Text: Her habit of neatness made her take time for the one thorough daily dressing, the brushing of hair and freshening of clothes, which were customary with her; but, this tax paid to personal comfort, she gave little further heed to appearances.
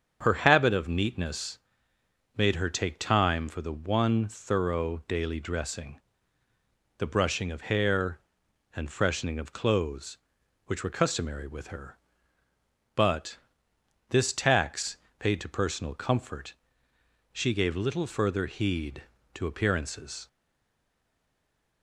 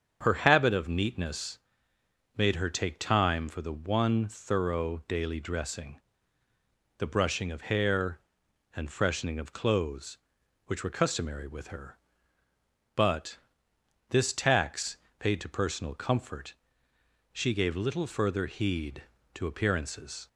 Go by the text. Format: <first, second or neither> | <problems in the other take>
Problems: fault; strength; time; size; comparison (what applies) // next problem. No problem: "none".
second | starts louder than the rest; strong; until 1.2 s; 7 dB; strong in the second // pauses between "neatness" and "made"; noticeable; at 1.5 s; 0.80 s long; noticeable in the second // pauses between "tax" and "paid"; slight; at 14.9 s; 0.20 s long; slight in the second // stays silent after the last word; noticeable; from 20.2 s on; 1.6 s long